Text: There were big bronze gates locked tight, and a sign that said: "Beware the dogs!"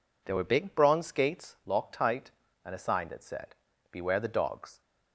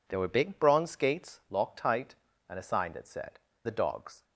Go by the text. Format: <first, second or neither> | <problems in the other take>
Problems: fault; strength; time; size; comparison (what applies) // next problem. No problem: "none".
first | skips "Beware"; at 3.5 s